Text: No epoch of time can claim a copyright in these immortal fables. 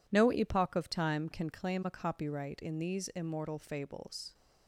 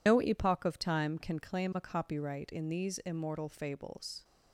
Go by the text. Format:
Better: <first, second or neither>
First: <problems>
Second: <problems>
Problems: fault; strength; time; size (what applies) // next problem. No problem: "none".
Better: first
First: none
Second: loses the start of "No"; at 0.0 s; 75 ms